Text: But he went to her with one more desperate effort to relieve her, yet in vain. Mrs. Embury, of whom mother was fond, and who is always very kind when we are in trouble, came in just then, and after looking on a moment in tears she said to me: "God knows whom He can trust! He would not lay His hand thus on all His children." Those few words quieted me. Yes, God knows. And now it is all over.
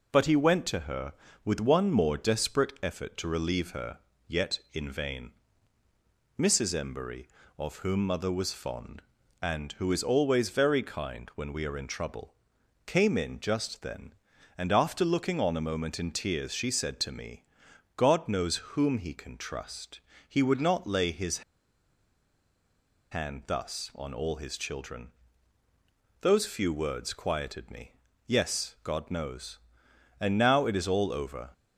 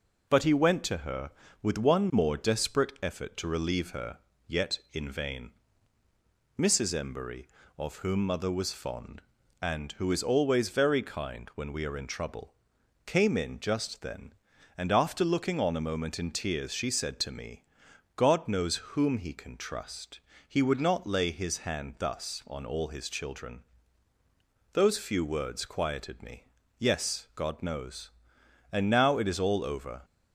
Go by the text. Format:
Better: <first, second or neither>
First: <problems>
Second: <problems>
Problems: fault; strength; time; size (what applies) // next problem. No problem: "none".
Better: second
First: pauses between "knows" and "whom"; slight; at 18.5 s; 0.16 s long // pauses between "His" and "hand"; strong; at 21.4 s; 1.7 s long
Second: pauses between "knows" and "whom"; slight; at 18.7 s; 0.16 s long